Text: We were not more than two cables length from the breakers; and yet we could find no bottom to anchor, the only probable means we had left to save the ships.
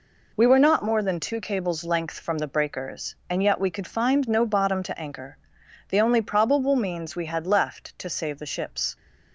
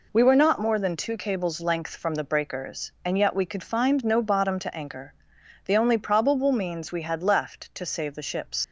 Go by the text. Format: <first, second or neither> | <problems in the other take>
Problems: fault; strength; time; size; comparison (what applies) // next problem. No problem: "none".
first | leaves "ships" unfinished; at 8.6 s; 75 ms